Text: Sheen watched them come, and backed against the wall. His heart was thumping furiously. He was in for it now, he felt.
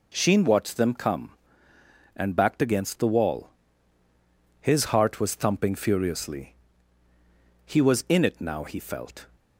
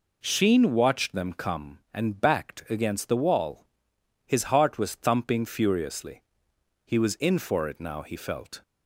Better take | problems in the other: second | skips "for"; at 8.2 s

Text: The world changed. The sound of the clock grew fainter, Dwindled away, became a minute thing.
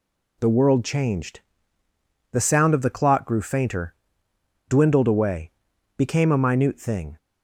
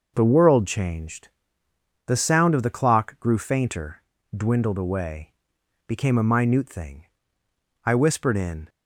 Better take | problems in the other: first | goes on to say "I whispered in"; noticeable; from 7.8 s on; 0.84 s long

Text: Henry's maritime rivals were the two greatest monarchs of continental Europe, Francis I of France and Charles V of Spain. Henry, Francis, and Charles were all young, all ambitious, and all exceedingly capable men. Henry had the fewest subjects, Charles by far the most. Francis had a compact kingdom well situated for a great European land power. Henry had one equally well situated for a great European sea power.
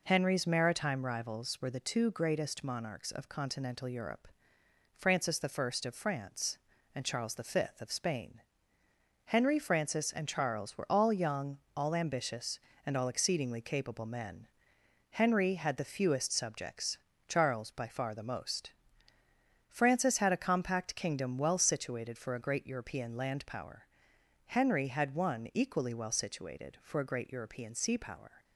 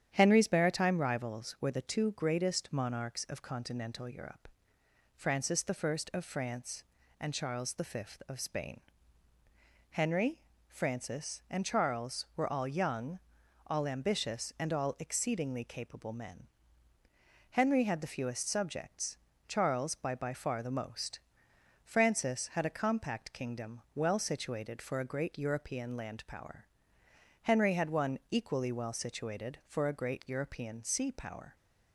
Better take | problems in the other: first | starts louder than the rest; strong; until 1.1 s; 9.5 dB // says "by" twice; at 20.1 s

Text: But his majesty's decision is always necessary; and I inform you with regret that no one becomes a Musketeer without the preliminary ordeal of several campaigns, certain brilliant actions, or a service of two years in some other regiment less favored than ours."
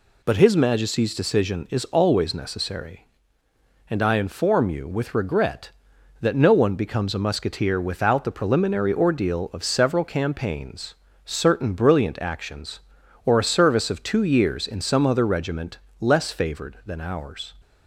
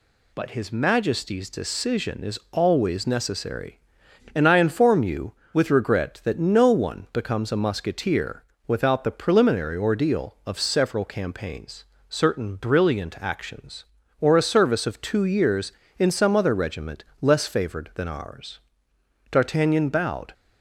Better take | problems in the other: first | pauses between "Musketeer" and "without"; slight; at 8.4 s; 0.24 s long // pauses between "regiment" and "less"; slight; at 17.0 s; 0.16 s long; slight in the first // goes on to say "D'Artagnan bowed"; noticeable; from 19.3 s on; 1.0 s long

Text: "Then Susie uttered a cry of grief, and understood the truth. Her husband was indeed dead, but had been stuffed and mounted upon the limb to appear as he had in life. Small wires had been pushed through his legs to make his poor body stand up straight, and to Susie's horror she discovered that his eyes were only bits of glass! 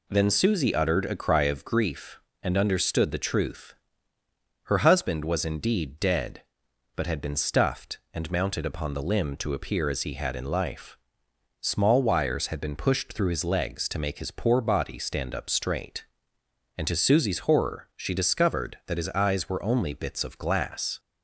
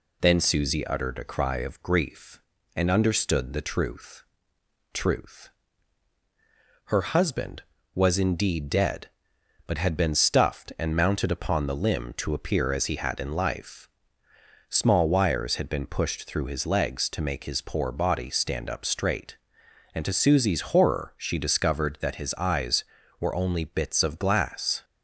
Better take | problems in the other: first | says "truth" twice; at 4.9 s

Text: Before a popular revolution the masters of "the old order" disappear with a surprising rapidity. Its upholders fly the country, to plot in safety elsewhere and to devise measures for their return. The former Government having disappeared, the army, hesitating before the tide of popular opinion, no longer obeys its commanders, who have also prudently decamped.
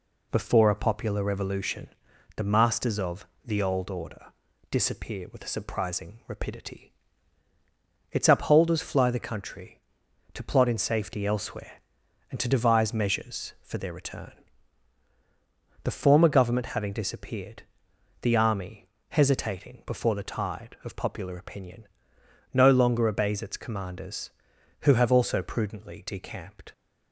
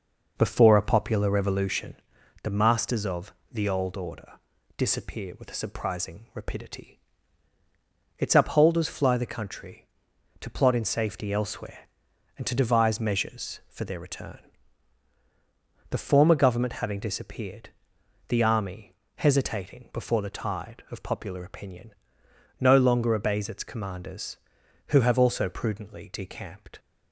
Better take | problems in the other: first | starts louder than the rest; noticeable; until 1.9 s; 5.5 dB // pauses between "revolution" and "the"; noticeable; at 1.9 s; 0.48 s long; noticeable in the first // pauses between "of" and "the"; slight; at 3.3 s; 0.18 s long; slight in the first // pauses between "order" and "disappear"; at 4.3 s; 0.44 s long; also in the first

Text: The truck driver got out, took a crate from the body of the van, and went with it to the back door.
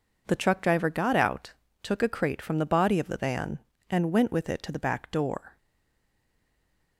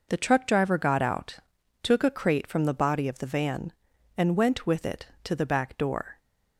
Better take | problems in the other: second | stays silent after the last word; noticeable; from 5.5 s on; 1.4 s long

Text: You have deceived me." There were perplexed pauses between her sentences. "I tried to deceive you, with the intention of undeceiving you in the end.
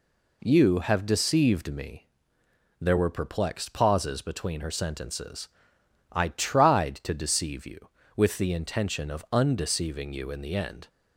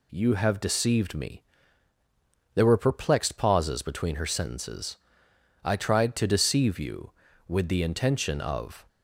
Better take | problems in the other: first | stops before "undeceiving you in the end"; at 8.8 s

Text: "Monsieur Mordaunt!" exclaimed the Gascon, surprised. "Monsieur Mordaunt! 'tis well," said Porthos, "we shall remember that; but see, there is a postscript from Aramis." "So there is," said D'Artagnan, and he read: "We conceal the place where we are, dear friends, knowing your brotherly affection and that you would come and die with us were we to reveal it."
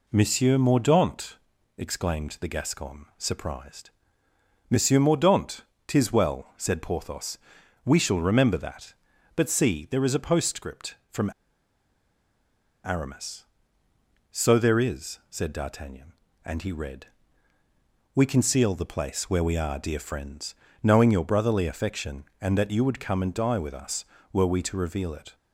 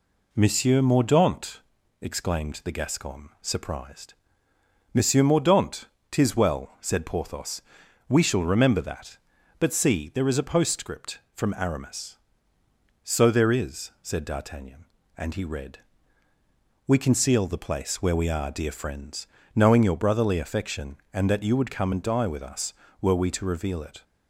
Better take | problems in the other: second | pauses between "from" and "Aramis"; strong; at 11.2 s; 1.5 s long

